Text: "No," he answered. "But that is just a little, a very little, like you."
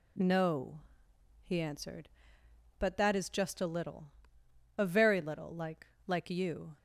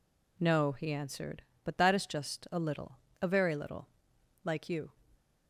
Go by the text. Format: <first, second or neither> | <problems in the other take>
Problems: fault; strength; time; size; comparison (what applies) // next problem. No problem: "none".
second | says "like" twice; at 6.0 s